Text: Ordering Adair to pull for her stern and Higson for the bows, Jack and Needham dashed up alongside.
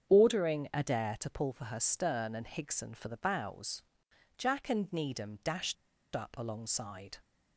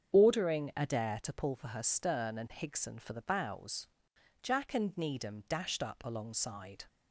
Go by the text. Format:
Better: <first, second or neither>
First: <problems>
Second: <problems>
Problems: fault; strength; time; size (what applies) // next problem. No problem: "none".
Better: second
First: starts louder than the rest; strong; until 1.1 s; 7.5 dB // pauses between "dashed" and "up"; at 5.7 s; 0.40 s long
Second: starts louder than the rest; strong; until 1.1 s; 7.5 dB